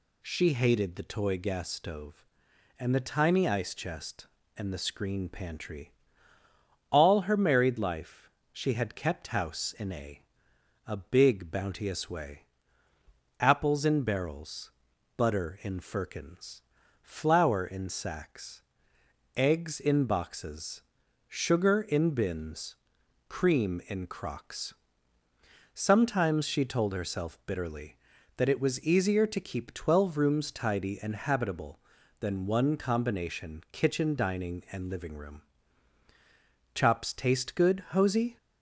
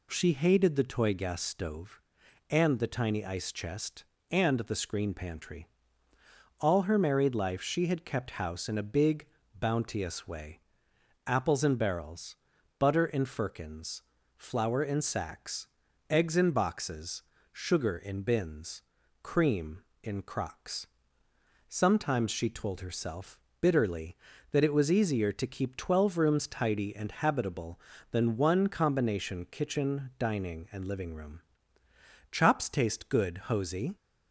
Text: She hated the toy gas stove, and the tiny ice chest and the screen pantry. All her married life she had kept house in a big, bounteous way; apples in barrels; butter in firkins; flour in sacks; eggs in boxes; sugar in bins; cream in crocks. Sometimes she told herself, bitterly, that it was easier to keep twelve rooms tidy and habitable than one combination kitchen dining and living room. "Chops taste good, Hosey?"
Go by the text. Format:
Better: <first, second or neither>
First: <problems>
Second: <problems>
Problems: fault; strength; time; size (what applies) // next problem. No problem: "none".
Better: second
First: pauses between "life" and "she"; slight; at 8.2 s; 0.24 s long // says "a" twice; at 10.8 s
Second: none